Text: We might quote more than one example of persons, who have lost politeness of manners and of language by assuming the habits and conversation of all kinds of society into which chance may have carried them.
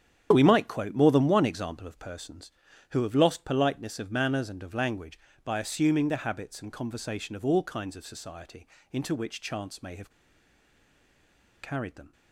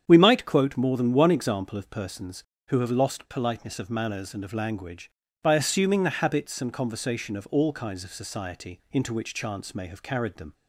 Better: second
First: starts louder than the rest; strong; until 1.3 s; 9 dB // pauses between "society" and "into"; slight; at 8.6 s; 0.28 s long // pauses between "have" and "carried"; strong; at 10.0 s; 1.5 s long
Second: starts louder than the rest; strong; until 1.0 s; 8 dB

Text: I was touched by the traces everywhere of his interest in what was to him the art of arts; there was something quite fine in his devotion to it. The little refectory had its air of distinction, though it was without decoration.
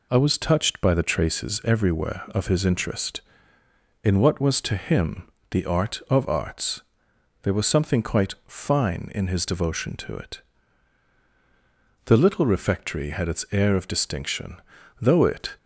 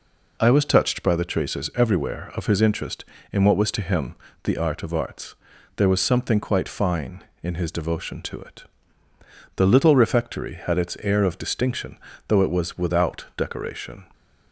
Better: second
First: pauses between "him" and "the"; slight; at 5.2 s; 0.20 s long // stops before "was without decoration"; at 15.5 s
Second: pauses between "him" and "the"; slight; at 4.1 s; 0.30 s long

